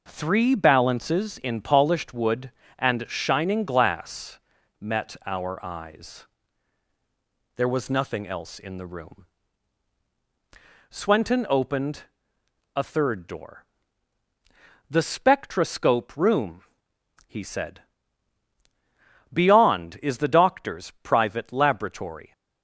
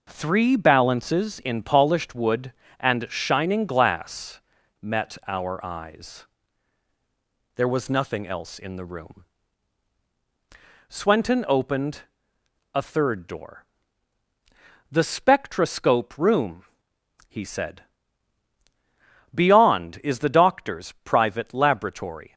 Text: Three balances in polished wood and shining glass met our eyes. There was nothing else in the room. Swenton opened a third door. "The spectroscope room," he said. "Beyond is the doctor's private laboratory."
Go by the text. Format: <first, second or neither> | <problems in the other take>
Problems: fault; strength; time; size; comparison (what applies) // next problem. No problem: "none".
neither | pauses between "glass" and "met"; the same in both // pauses between "opened" and "a"; noticeable; the same in both